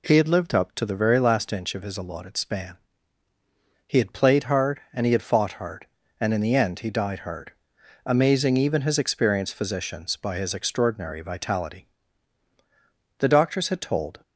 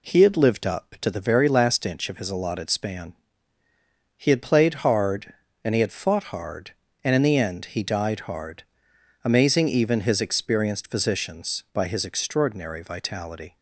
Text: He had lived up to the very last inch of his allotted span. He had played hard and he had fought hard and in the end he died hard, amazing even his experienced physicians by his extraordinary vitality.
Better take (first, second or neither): second